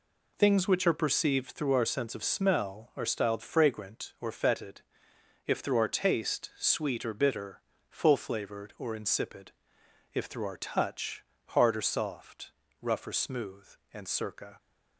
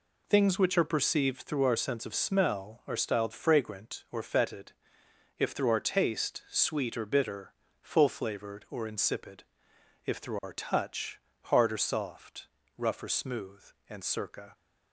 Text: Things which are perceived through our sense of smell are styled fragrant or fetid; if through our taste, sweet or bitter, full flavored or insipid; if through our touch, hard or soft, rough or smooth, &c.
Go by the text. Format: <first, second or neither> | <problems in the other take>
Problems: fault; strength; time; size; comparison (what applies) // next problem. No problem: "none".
neither | none